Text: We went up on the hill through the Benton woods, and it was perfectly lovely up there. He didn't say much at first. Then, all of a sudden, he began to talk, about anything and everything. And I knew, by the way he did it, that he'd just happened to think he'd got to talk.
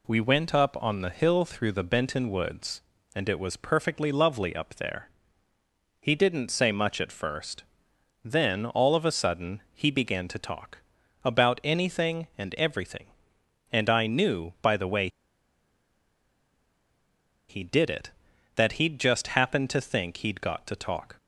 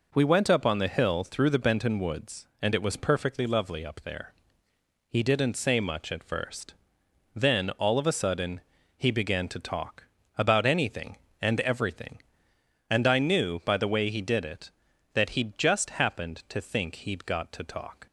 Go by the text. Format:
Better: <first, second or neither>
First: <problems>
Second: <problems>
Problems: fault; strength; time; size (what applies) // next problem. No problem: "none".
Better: second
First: pauses between "way" and "he"; strong; at 15.0 s; 2.4 s long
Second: none